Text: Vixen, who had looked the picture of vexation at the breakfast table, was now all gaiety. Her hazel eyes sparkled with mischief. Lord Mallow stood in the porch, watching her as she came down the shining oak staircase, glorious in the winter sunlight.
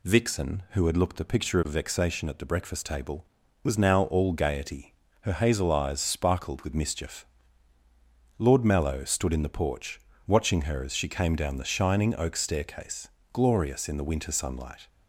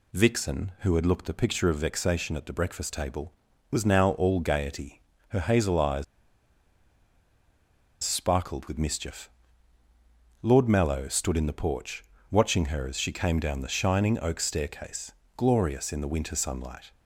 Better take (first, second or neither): first